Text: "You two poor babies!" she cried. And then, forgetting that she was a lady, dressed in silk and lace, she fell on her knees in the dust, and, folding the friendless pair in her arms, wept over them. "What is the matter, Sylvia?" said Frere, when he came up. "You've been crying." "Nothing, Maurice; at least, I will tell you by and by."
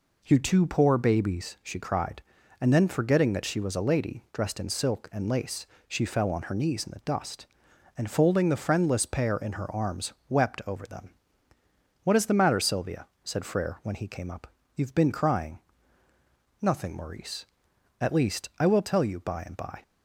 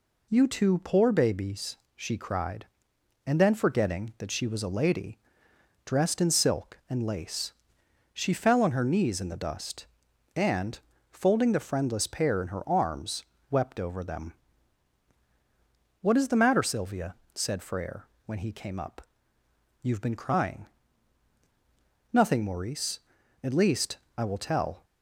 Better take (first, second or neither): first